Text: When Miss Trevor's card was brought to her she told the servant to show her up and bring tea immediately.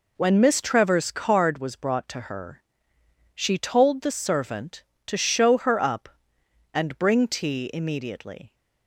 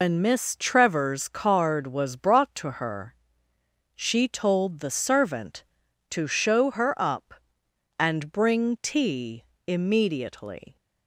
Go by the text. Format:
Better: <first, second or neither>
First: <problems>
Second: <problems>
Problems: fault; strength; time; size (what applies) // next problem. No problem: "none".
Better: first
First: pauses between "her" and "she"; noticeable; at 2.6 s; 0.76 s long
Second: loses the start of "When"; at 0.0 s; 150 ms // pauses between "her" and "she"; noticeable; at 3.1 s; 0.80 s long // pauses between "tea" and "immediately"; slight; at 9.4 s; 0.24 s long